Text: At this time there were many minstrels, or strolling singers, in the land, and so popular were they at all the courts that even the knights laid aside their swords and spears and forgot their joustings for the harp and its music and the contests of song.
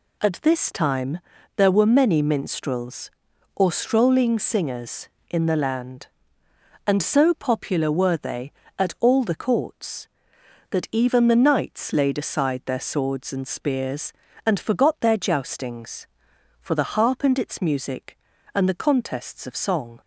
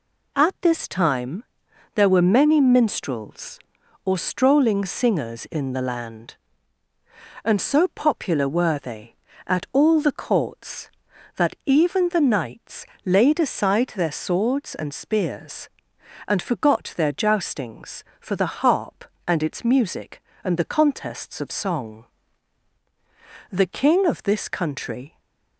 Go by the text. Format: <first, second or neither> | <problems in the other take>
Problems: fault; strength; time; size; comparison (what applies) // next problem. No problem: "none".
first | pauses between "time" and "there"; noticeable; at 1.4 s; 0.50 s long; also in the first // pauses between "knights" and "laid"; slight; at 12.8 s; 0.18 s long // goes on to say "The King of this country"; from 23.5 s on; 1.6 s long // stays silent after the last word; slight; from 25.0 s on; 0.5 s long